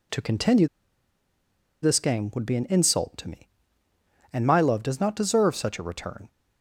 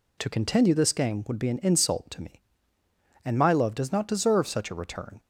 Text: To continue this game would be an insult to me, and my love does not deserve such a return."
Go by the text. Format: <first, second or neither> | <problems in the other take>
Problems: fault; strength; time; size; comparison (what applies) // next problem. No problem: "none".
second | pauses between "continue" and "this"; at 0.6 s; 1.1 s long